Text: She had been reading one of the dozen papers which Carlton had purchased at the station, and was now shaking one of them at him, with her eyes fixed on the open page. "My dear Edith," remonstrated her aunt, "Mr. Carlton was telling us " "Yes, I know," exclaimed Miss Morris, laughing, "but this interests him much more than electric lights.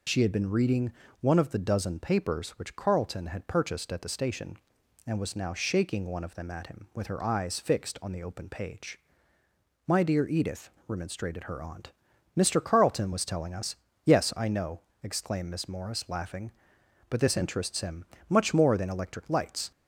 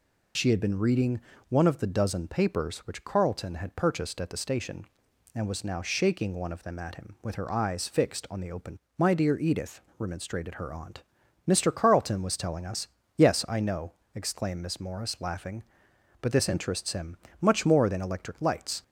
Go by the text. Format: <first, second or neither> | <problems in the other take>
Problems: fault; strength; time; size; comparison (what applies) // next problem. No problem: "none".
first | pauses between "reading" and "one"; slight; at 1.2 s; 0.26 s long; slight in the first // skips "page"; at 8.8 s // pauses between "him" and "much"; slight; at 17.1 s; 0.24 s long; slight in the first